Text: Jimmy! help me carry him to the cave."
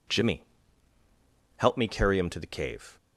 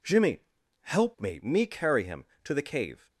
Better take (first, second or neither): first